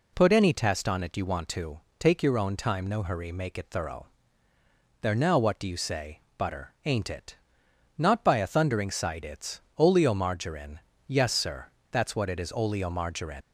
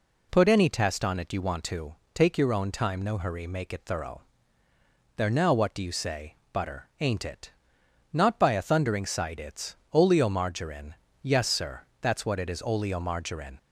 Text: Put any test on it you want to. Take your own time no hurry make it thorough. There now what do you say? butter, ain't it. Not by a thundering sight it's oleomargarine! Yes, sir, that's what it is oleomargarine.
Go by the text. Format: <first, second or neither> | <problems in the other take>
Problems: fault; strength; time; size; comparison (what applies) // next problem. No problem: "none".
second | pauses between "it's" and "oleomargarine"; slight; at 9.6 s; 0.18 s long; slight in the second // leaves "oleomargarine" unfinished; at 13.4 s; 65 ms